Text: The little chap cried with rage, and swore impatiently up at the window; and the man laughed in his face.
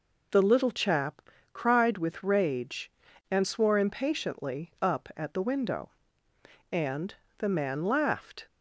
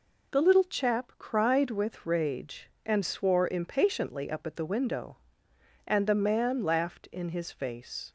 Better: second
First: pauses between "chap" and "cried"; slight; at 1.2 s; 0.32 s long // pauses between "and" and "the"; slight; at 7.1 s; 0.22 s long // stops before "in his face"; at 8.4 s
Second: none

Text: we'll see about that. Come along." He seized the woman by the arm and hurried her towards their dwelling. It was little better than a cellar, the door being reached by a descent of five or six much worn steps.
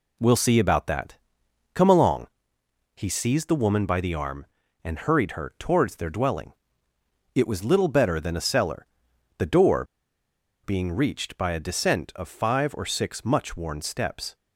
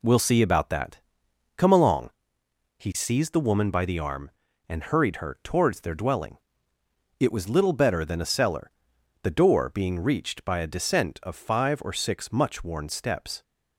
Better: second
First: pauses between "door" and "being"; noticeable; at 9.8 s; 0.79 s long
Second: none

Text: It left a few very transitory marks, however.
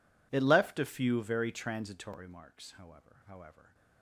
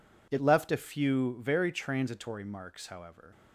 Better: second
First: says "however" twice; at 3.2 s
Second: none

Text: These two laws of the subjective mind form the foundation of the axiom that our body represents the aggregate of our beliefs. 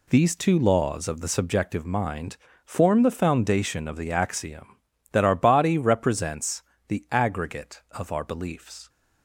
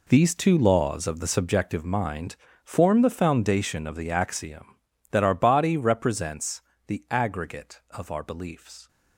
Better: first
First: pauses between "mind" and "form"; slight; at 2.3 s; 0.28 s long // pauses between "represents" and "the"; slight; at 6.6 s; 0.24 s long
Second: gets quieter; strong; throughout; 13 dB // pauses between "mind" and "form"; slight; at 2.3 s; 0.28 s long // pauses between "represents" and "the"; slight; at 6.6 s; 0.24 s long

